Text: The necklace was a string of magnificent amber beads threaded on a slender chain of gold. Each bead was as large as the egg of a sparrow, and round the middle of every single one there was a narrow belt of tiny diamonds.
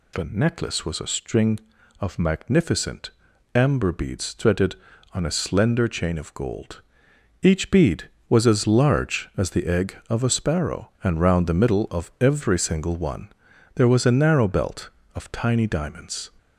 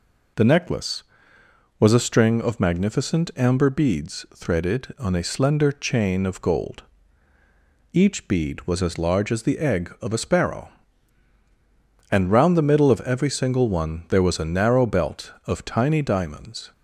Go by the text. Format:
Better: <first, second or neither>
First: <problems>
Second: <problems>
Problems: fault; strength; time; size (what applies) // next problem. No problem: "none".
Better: second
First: gets louder; slight; throughout; 2.5 dB // pauses between "magnificent" and "amber"; at 3.1 s; 0.42 s long // pauses between "one" and "there"; noticeable; at 13.2 s; 0.46 s long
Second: none